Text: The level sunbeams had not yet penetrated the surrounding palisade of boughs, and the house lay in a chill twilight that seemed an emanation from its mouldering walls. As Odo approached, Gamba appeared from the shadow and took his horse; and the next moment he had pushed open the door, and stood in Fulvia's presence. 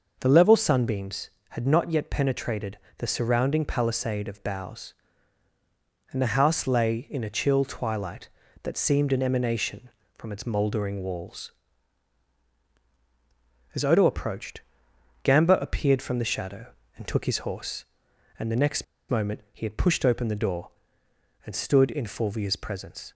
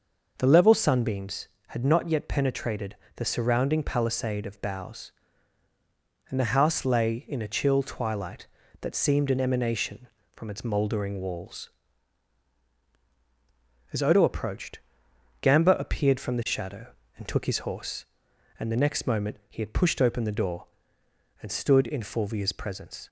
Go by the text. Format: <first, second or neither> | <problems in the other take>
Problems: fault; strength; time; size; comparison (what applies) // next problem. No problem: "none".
second | pauses between "penetrated" and "the"; slight; at 2.7 s; 0.20 s long; slight in the second // pauses between "next" and "moment"; slight; at 18.8 s; 0.24 s long